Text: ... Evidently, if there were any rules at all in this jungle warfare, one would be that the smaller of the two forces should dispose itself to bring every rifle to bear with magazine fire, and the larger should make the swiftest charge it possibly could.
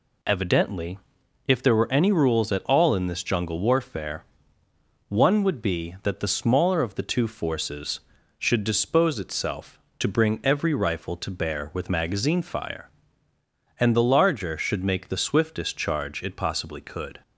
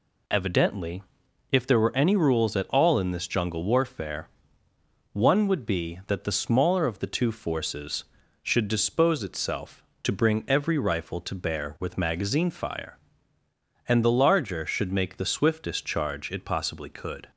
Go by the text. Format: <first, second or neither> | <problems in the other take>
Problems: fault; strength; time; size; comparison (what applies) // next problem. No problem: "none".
neither | none